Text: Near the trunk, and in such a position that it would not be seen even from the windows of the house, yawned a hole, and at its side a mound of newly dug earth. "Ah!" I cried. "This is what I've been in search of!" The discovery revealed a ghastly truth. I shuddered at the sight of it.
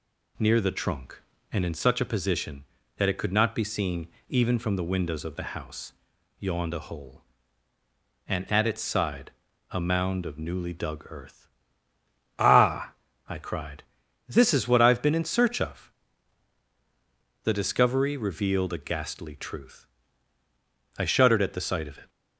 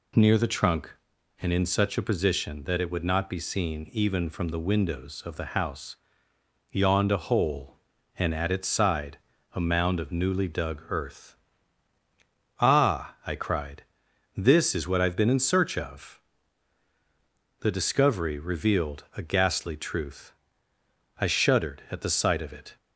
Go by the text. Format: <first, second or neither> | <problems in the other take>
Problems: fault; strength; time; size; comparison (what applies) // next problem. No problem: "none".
second | says "could" for "would"; at 3.1 s // pauses between "seen" and "even"; slight; at 4.0 s; 0.18 s long // pauses between "side" and "a"; at 9.3 s; 0.40 s long; slight in the second